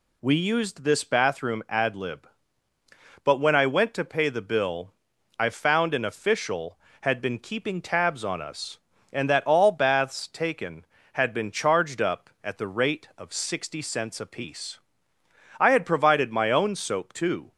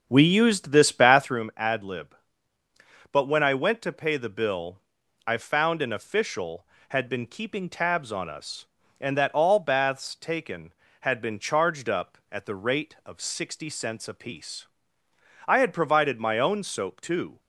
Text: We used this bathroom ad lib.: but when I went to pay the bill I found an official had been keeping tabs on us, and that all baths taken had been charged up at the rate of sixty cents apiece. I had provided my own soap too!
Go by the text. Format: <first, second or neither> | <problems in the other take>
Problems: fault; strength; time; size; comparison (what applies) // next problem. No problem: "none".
first | starts louder than the rest; until 1.4 s; 6.5 dB // pauses between "bill" and "I"; noticeable; at 4.7 s; 0.50 s long; noticeable in the first